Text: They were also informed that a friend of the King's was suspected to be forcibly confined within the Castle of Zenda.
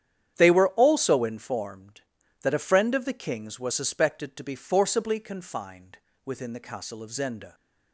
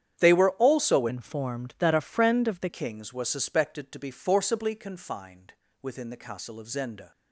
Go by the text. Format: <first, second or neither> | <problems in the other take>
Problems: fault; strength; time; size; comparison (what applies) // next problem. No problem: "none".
first | starts louder than the rest; strong; until 1.2 s; 9.5 dB; strong in the first // changes voice from "informed" to "the"; from 1.0 to 2.6 s; 1.6 s long // pauses between "confined" and "within"; slight; at 5.5 s; 0.28 s long; slight in the first